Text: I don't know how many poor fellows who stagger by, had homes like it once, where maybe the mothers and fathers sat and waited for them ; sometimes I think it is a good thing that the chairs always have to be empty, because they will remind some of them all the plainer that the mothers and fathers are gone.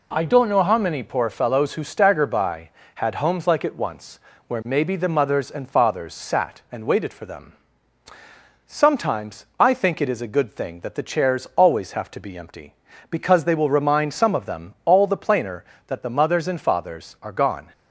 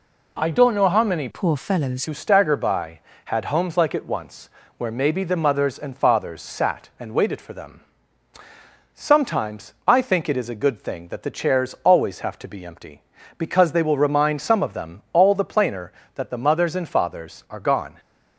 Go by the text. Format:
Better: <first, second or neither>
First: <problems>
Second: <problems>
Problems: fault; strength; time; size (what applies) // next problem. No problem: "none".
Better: first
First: none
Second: changes voice from "poor" to "fellows"; from 1.3 to 2.0 s; 0.7 s long